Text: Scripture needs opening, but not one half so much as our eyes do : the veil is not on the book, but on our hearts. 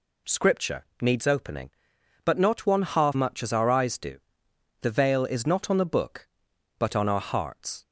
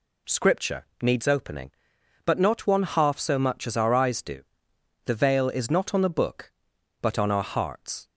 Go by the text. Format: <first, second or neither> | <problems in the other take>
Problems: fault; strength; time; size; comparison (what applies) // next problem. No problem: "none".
second | pauses between "Scripture" and "needs"; slight; at 0.8 s; 0.18 s long; slight in the second // skips "so"; at 3.1 s